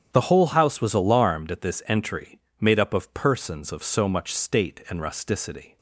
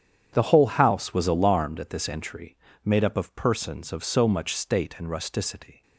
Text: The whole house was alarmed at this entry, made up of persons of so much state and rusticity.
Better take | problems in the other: neither | starts louder than the rest; strong; the same in both

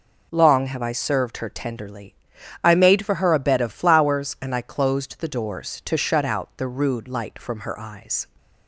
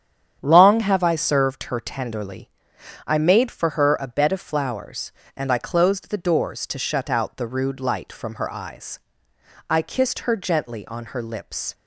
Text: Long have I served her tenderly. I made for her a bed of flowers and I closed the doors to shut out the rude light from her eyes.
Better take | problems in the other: first | starts louder than the rest; strong; until 1.4 s; 9 dB // goes on to say "I kissed her gently on her lips"; strong; from 9.6 s on; 2.0 s long

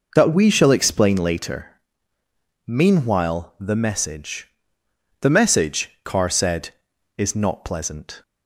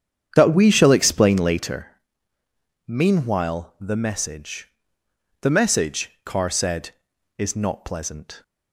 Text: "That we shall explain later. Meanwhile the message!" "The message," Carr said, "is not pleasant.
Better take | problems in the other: first | starts louder than the rest; strong; until 1.8 s; 8 dB

